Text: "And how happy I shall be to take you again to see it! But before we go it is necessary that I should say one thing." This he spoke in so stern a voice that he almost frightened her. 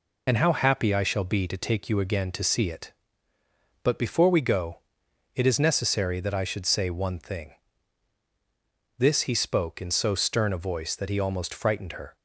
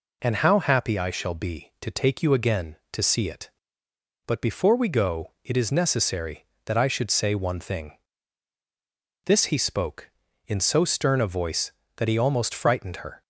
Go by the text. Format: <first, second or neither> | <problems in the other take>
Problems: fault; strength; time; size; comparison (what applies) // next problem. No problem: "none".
second | loses the start of "And"; at 0.2 s; 35 ms // pauses between "go" and "it"; noticeable; at 4.7 s; 0.56 s long